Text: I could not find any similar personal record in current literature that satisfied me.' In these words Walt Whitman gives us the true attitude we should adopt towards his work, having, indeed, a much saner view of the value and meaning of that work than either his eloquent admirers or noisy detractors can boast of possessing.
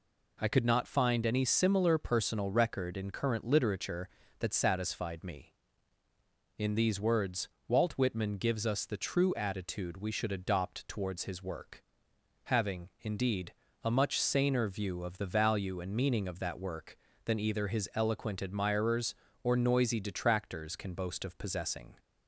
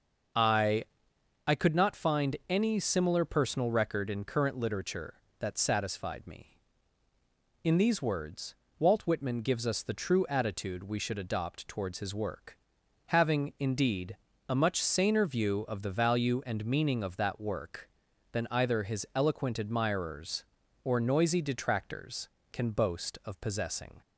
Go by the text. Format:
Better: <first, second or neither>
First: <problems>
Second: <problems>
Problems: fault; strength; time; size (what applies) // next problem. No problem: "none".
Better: first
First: pauses between "words" and "Walt"; slight; at 7.4 s; 0.18 s long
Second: starts louder than the rest; noticeable; until 1.9 s; 6 dB // says "I" twice; at 1.4 s // pauses between "words" and "Walt"; slight; at 8.5 s; 0.24 s long